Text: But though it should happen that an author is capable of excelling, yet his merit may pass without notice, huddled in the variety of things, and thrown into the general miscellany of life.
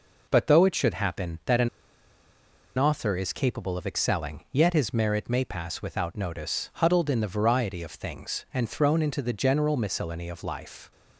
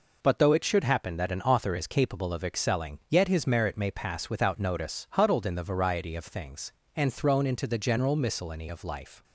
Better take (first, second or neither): second